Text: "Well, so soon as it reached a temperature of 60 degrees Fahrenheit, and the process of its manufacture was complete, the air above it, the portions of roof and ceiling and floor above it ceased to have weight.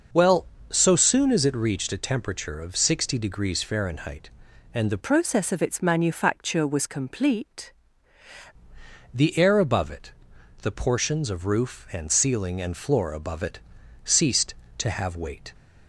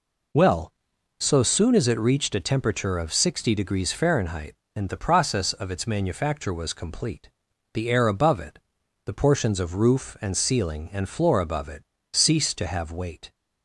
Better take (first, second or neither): second